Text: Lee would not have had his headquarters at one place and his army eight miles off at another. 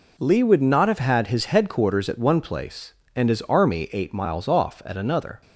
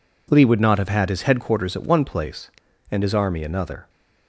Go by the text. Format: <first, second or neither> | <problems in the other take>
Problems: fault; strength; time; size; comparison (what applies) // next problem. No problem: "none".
first | skips "eight miles off at"; at 3.4 s